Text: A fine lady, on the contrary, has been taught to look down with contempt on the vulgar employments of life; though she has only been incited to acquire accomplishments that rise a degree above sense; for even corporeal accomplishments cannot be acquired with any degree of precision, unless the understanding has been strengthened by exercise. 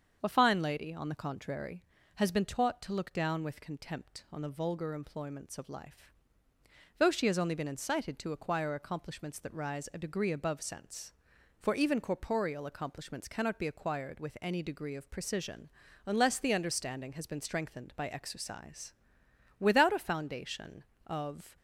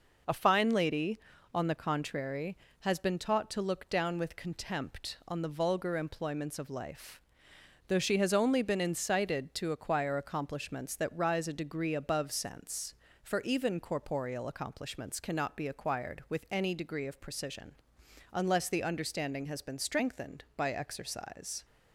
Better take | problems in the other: second | starts louder than the rest; strong; until 1.2 s; 7 dB // goes on to say "Without a foundation of"; strong; from 19.5 s on; 2.0 s long

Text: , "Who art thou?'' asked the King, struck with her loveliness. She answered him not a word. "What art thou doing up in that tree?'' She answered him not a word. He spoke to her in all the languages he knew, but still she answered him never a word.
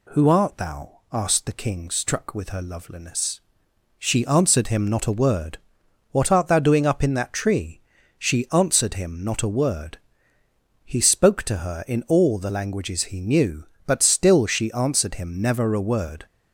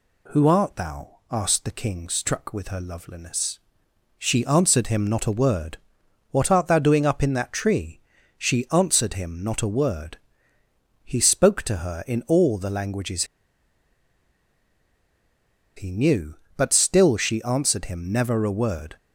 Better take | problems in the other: first | pauses between "languages" and "he"; strong; at 13.2 s; 2.5 s long

